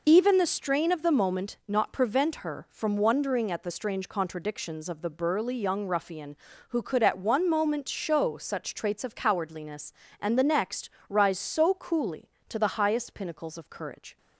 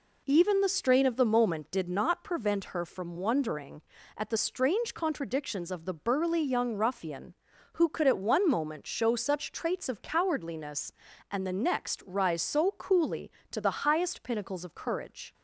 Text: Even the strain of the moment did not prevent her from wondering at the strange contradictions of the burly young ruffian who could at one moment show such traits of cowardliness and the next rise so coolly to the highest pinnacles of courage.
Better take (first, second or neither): second